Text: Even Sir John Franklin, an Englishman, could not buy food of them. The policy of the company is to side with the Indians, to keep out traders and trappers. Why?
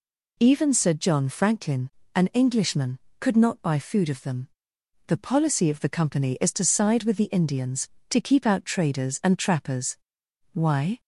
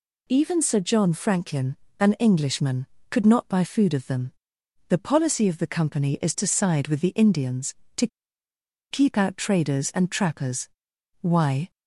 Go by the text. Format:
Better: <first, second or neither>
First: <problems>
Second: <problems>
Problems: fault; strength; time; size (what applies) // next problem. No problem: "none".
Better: first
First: none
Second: pauses between "to" and "keep"; noticeable; at 8.0 s; 0.84 s long